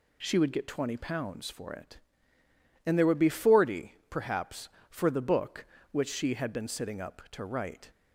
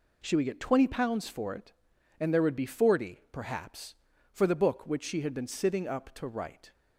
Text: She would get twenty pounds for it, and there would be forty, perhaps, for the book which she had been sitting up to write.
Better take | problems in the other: neither | none

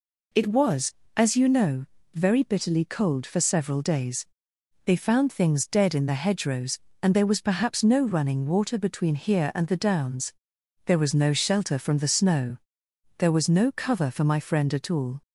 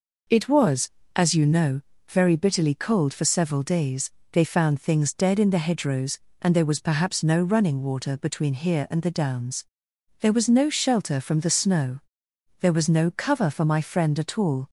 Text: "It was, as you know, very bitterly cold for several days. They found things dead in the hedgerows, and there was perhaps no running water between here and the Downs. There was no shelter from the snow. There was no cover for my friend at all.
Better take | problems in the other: neither | none

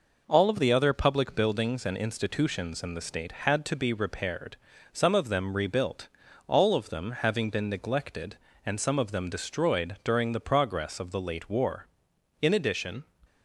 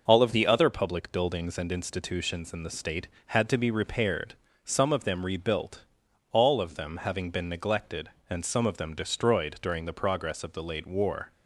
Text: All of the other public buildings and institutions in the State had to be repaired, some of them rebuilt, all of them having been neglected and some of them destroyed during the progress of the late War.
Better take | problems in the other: second | goes on to say "In addition"; noticeable; from 12.4 s on; 0.64 s long

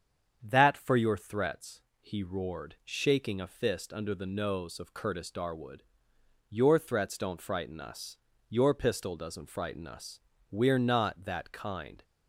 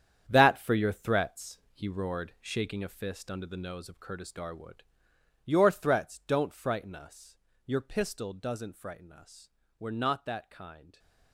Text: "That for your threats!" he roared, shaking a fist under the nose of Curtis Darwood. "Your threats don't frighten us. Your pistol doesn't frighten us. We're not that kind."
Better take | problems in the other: first | gets quieter; strong; throughout; 10.5 dB // starts louder than the rest; strong; until 1.2 s; 9 dB; strong in the first

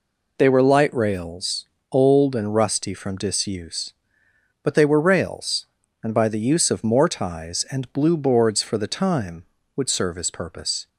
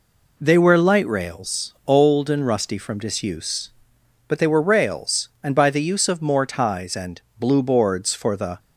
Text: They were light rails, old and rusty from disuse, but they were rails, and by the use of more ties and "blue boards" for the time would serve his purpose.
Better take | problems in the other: first | pauses between "and" and "blue"; slight; at 7.2 s; 0.18 s long // stops before "time would serve his purpose"; at 8.5 s

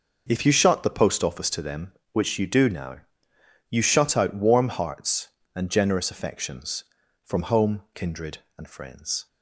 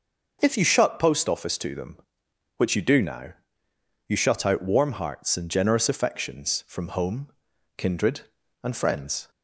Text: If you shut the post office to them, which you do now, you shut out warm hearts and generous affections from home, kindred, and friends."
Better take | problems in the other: first | skips "the"; at 0.9 s

